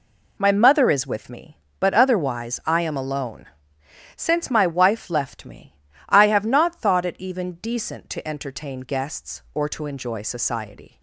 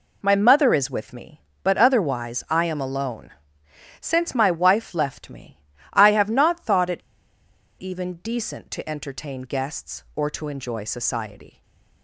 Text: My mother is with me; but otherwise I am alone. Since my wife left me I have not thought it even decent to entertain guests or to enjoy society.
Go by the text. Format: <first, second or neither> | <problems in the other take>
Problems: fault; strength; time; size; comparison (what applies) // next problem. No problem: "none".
first | pauses between "me" and "I"; slight; at 5.6 s; 0.30 s long; slight in the first // pauses between "it" and "even"; noticeable; at 6.9 s; 0.79 s long // stays silent after the last word; slight; from 11.5 s on; 0.5 s long